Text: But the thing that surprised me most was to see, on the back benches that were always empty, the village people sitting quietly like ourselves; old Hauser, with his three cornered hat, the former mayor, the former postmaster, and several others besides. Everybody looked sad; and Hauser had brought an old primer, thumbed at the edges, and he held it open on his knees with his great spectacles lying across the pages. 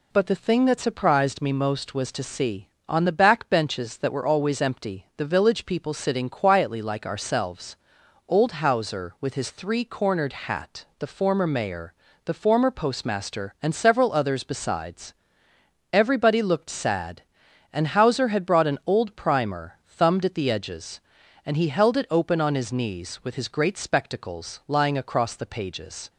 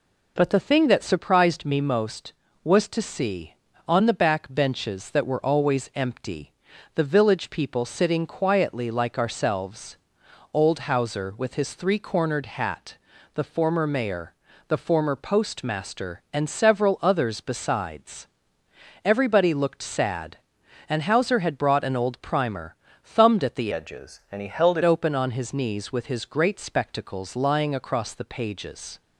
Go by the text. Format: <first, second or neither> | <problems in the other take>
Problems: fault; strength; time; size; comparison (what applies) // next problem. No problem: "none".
first | changes voice from "edges" to "it"; from 23.7 to 24.8 s; 1.1 s long